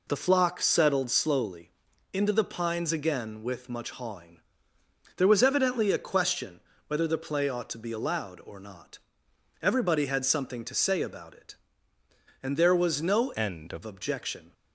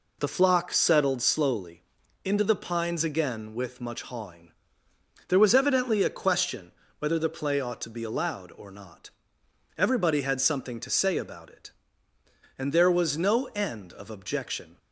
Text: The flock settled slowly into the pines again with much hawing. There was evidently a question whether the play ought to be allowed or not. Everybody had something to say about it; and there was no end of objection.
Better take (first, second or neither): second